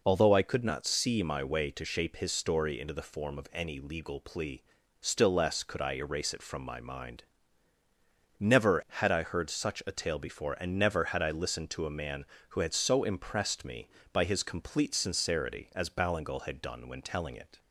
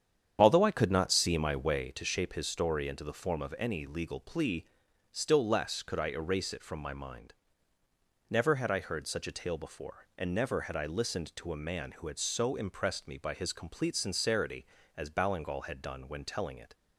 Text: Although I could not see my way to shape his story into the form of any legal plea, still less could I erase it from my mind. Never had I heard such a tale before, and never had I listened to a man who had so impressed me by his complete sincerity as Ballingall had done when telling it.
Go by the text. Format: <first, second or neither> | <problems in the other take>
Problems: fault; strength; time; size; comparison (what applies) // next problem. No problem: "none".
first | starts louder than the rest; strong; until 1.9 s; 8.5 dB